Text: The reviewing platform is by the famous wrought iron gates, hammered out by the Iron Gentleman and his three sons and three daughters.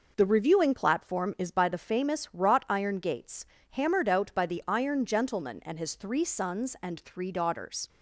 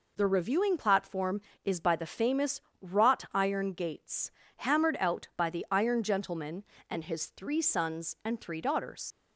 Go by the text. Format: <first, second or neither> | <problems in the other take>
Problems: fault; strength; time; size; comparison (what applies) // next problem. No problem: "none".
first | pauses between "famous" and "wrought"; slight; at 2.5 s; 0.22 s long // leaves "daughters" unfinished; at 9.1 s; 75 ms